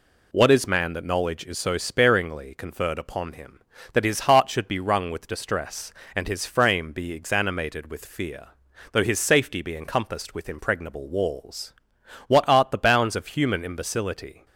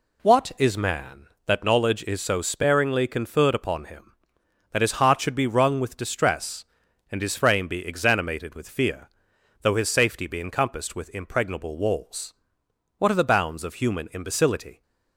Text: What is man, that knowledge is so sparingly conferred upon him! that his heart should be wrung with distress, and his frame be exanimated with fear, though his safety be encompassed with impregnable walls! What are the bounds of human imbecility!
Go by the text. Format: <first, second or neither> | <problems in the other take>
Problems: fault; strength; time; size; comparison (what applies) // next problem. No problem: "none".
second | says "art" for "are"; at 12.4 s